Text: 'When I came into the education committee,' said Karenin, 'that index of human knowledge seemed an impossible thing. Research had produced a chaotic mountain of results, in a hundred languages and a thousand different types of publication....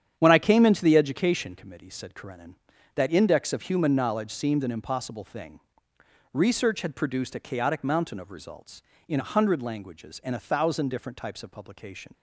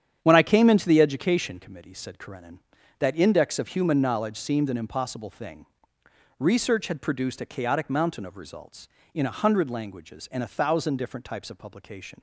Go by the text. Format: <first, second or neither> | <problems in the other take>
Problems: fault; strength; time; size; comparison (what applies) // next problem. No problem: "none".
neither | starts louder than the rest; strong; the same in both